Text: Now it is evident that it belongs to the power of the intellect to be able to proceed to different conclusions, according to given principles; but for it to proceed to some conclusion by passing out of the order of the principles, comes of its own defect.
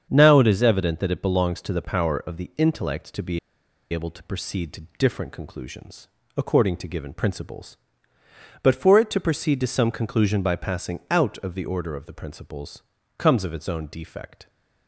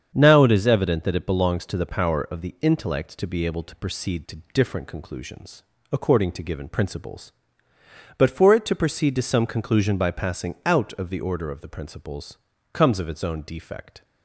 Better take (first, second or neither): second